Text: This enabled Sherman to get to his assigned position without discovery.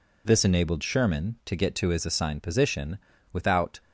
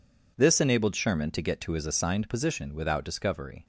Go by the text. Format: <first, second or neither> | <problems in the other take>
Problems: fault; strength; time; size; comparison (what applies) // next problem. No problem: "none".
second | pauses between "position" and "without"; at 2.9 s; 0.38 s long // stops before "discovery"; at 3.8 s